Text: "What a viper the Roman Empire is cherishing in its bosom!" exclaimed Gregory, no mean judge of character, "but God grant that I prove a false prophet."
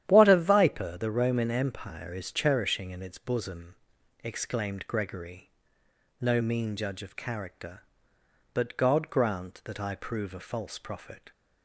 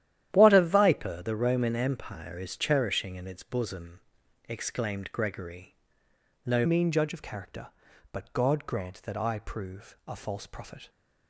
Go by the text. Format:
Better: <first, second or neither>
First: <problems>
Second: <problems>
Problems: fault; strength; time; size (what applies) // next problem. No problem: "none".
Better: first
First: starts louder than the rest; strong; until 1.0 s; 11 dB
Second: starts louder than the rest; strong; until 1.3 s; 11.5 dB // changes voice at "mean"; from 6.6 s on; 4.2 s long